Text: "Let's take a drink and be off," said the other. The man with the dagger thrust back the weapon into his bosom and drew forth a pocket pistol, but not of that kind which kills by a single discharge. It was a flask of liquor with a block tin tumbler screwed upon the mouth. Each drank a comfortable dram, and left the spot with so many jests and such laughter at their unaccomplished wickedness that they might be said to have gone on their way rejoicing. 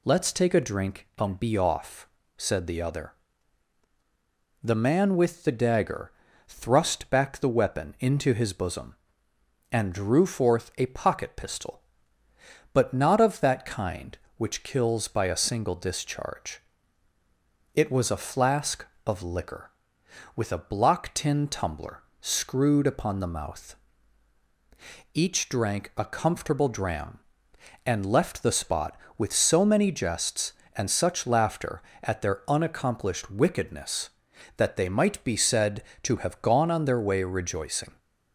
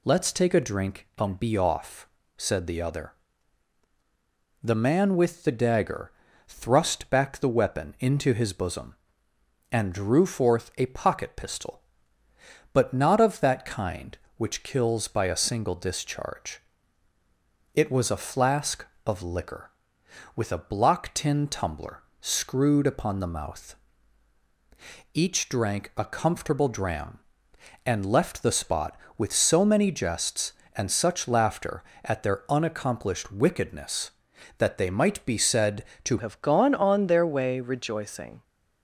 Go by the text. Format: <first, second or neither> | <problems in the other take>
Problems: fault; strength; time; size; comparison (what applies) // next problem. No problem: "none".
first | pauses between "dagger" and "thrust"; slight; at 6.1 s; 0.36 s long; slight in the first // pauses between "tumbler" and "screwed"; slight; at 22.0 s; 0.18 s long; slight in the first // changes voice at "have"; from 36.1 s on; 2.3 s long